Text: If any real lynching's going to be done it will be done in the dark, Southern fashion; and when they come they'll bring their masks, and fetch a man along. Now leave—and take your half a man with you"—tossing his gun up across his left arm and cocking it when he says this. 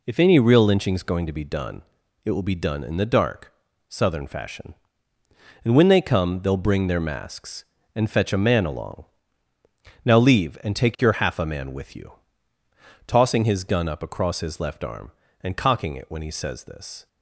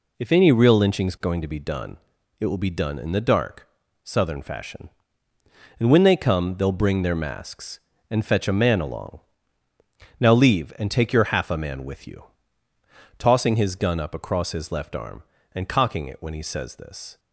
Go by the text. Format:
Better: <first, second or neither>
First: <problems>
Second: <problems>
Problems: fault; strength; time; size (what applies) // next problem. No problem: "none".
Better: neither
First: pauses between "done" and "it"; at 1.8 s; 0.42 s long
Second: pauses between "done" and "it"; at 1.9 s; 0.42 s long